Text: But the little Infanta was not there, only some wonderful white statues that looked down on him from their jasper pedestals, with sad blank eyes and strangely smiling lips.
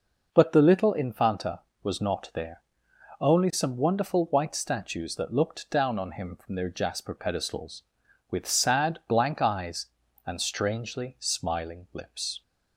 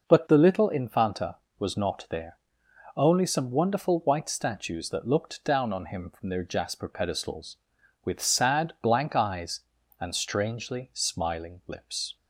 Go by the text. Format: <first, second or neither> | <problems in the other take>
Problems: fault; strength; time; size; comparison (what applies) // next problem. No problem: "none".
neither | none